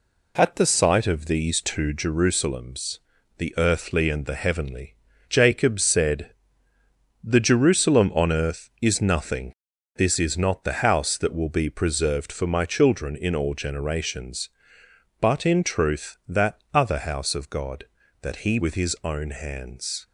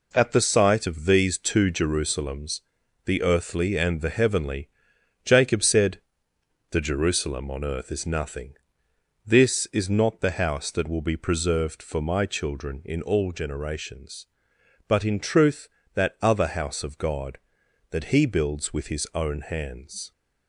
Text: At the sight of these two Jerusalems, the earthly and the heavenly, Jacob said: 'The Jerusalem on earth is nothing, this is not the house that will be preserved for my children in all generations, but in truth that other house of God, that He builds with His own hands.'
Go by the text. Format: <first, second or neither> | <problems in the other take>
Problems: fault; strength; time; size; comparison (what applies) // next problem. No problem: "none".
second | pauses between "that" and "other"; slight; at 16.5 s; 0.16 s long // skips "builds"; at 18.5 s